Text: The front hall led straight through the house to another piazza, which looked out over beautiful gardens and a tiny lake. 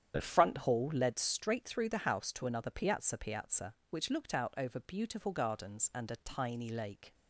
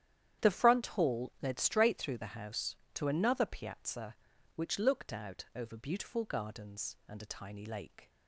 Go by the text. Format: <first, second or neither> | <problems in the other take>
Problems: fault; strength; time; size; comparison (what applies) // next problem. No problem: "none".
second | starts louder than the rest; strong; until 1.2 s; 9 dB; strong in the second // says "piazza" twice; at 3.1 s